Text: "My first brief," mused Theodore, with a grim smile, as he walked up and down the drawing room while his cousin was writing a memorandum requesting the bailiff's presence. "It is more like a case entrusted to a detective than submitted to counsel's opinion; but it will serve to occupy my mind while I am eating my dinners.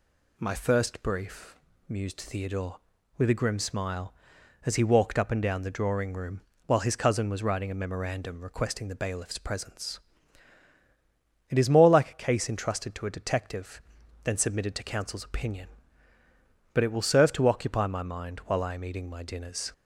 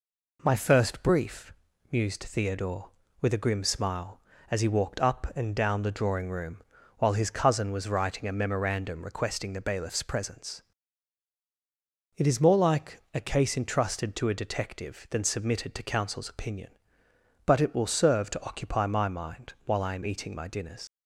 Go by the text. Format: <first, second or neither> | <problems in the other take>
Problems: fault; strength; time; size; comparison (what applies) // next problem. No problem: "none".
first | pauses between "room" and "while"; slight; at 6.6 s; 0.34 s long; slight in the first // leaves "dinners" unfinished; at 20.8 s; 90 ms